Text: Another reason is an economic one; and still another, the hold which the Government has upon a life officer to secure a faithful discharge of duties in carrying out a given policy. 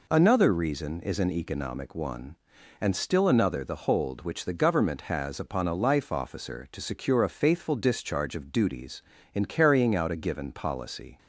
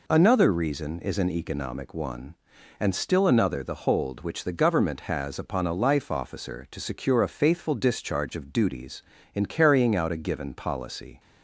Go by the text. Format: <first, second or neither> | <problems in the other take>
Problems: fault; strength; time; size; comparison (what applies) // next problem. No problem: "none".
neither | none